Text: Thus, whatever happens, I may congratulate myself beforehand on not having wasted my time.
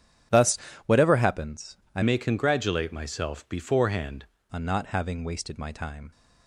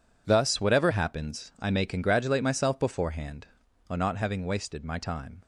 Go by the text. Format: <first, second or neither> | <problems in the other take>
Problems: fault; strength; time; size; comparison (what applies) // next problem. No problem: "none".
second | starts louder than the rest; strong; until 1.5 s; 10 dB // changes voice from "may" to "beforehand"; from 2.0 to 4.2 s; 2.2 s long